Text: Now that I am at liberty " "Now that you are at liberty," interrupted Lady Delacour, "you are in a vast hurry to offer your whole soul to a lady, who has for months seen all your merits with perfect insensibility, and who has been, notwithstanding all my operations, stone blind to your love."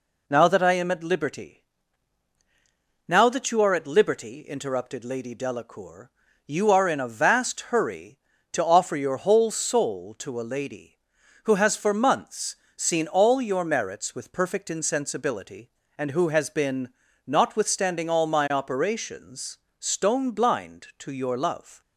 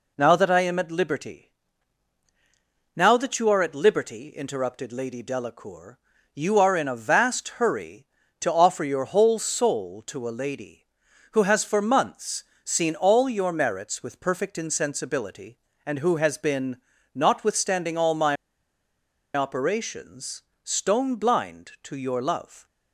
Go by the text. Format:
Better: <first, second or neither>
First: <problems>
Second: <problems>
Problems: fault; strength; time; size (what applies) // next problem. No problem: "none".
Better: first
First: pauses between "months" and "seen"; slight; at 12.5 s; 0.18 s long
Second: pauses between "months" and "seen"; slight; at 12.4 s; 0.18 s long // pauses between "my" and "operations"; at 18.3 s; 1.0 s long